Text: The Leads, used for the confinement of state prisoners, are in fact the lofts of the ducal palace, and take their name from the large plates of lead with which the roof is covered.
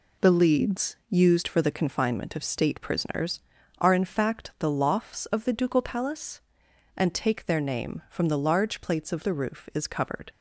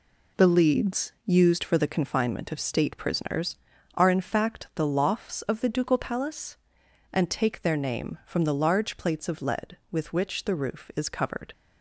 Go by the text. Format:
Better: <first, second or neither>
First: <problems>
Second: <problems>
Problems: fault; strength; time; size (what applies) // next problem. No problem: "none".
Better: second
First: skips "lead with which"; at 9.2 s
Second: none